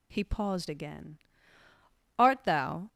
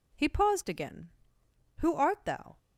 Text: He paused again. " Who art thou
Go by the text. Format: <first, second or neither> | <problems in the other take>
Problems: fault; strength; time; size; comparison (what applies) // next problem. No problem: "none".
second | skips "Who"; at 2.1 s